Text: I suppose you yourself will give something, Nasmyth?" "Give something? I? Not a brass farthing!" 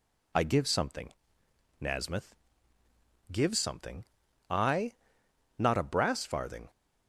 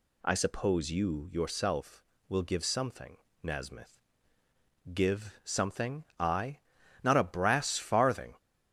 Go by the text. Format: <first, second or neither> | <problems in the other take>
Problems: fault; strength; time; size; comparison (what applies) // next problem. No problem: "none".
second | skips "suppose you yourself will"; at 0.4 s